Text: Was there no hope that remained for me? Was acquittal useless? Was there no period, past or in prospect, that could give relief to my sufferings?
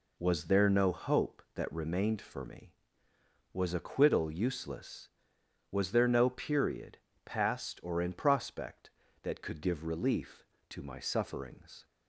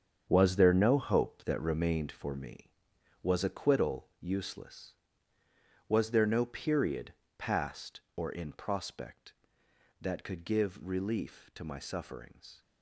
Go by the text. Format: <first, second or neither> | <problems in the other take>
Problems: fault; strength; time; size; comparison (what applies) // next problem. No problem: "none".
first | gets quieter; strong; throughout; 10 dB